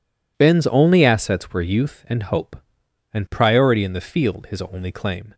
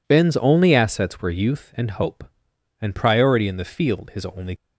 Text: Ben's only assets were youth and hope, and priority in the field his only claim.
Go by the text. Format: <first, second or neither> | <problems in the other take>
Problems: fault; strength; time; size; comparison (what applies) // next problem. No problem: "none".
first | stops before "claim"; at 4.5 s